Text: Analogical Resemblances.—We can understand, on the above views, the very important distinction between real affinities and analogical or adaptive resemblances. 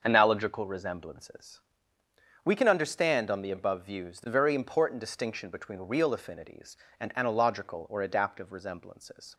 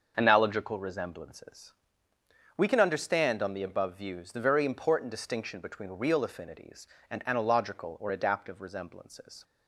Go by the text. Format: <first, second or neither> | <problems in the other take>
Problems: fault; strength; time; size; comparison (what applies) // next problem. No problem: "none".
neither | starts louder than the rest; the same in both